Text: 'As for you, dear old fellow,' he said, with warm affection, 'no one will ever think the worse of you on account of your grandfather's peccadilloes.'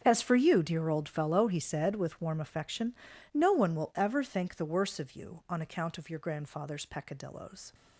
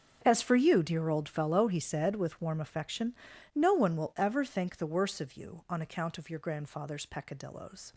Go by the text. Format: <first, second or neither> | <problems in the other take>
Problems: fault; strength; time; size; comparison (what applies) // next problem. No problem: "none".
neither | starts louder than the rest; strong; the same in both